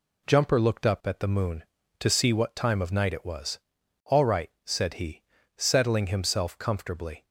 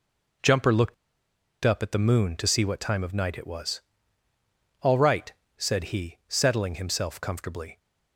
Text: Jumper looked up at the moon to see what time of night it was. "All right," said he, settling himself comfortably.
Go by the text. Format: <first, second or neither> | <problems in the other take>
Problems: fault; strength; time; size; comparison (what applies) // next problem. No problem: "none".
first | pauses between "looked" and "up"; noticeable; at 0.9 s; 0.70 s long